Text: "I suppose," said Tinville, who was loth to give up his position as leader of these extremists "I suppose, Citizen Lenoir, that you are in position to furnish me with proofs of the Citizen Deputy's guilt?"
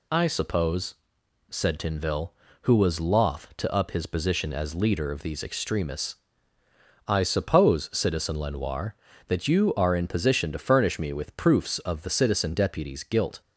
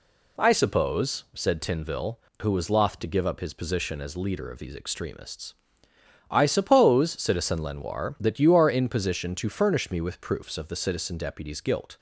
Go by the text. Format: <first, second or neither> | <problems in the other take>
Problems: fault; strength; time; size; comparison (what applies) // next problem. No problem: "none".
second | skips "give"; at 3.7 s // pauses between "extremists" and "I"; noticeable; at 6.1 s; 0.94 s long; noticeable in the second